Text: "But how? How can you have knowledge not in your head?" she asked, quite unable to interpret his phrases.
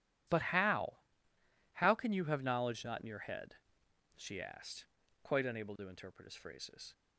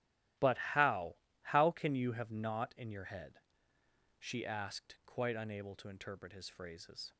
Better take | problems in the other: first | starts louder than the rest; strong; until 1.6 s; 13.5 dB // skips "knowledge"; at 2.3 s

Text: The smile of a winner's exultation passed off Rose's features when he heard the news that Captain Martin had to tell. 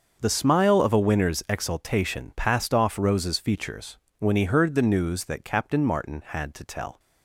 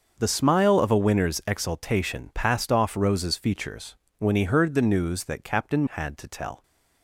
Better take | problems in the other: first | starts louder than the rest; until 1.1 s; 6.5 dB; also in the first // pauses between "features" and "when"; slight; at 3.9 s; 0.20 s long; slight in the first // skips "Martin"; at 5.8 s

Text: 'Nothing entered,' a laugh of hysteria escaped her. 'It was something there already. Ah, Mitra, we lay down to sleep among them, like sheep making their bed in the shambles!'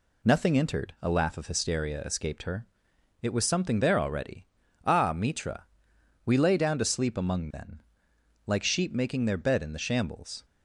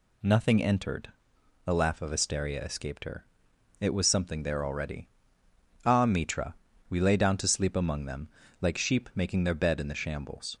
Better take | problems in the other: second | says "then" for "them"; at 7.5 s

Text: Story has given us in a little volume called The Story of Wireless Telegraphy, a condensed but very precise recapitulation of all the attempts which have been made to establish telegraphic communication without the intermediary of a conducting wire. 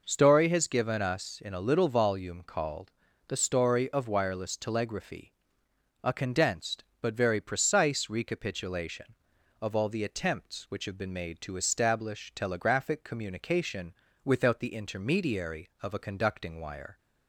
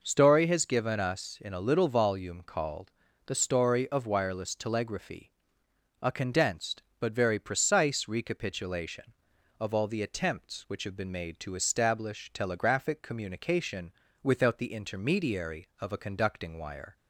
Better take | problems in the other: neither | pauses between "called" and "The"; slight; the same in both // pauses between "communication" and "without"; slight; the same in both

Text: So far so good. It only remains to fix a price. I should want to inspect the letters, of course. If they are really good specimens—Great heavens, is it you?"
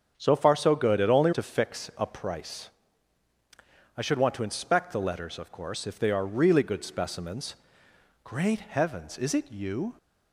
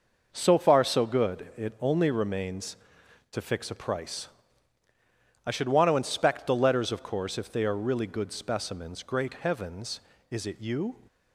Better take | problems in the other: second | starts louder than the rest; strong; until 1.1 s; 7.5 dB // skips "remains"; at 1.3 s

